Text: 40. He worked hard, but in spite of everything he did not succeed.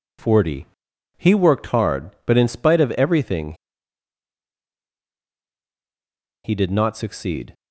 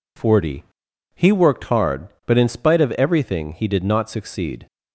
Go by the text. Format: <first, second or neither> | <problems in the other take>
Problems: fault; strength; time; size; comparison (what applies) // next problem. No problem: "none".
second | pauses between "everything" and "he"; strong; at 3.5 s; 2.9 s long